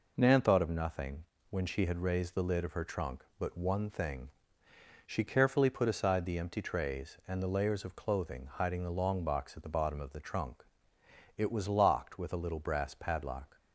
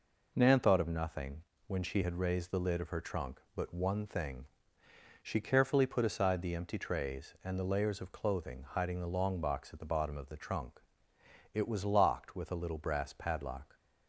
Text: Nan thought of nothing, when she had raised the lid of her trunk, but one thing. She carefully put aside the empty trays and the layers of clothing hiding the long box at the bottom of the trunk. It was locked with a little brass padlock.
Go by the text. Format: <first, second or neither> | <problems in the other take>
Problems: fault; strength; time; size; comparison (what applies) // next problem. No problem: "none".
neither | none